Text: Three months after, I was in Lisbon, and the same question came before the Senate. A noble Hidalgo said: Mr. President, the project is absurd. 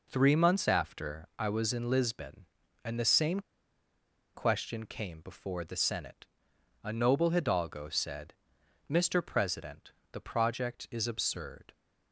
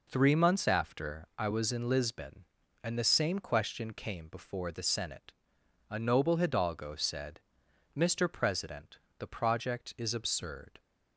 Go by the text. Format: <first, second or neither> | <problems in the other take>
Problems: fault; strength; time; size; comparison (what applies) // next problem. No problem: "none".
second | pauses between "same" and "question"; noticeable; at 3.4 s; 0.93 s long